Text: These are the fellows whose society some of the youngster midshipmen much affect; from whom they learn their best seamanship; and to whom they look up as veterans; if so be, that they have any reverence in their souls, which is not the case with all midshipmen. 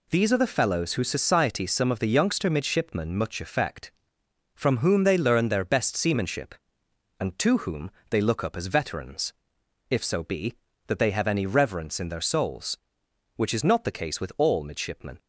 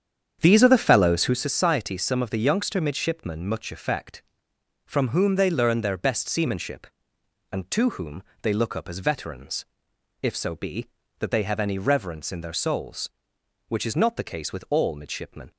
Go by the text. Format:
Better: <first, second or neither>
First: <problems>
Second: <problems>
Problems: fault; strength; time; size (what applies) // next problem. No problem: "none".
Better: first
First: pauses between "whom" and "they"; slight; at 7.8 s; 0.20 s long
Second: starts louder than the rest; strong; until 1.4 s; 8 dB // pauses between "whom" and "they"; slight; at 8.2 s; 0.20 s long